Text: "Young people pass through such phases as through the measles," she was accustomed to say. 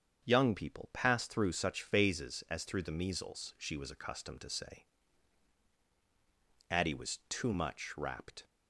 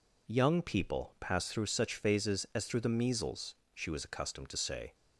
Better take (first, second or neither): second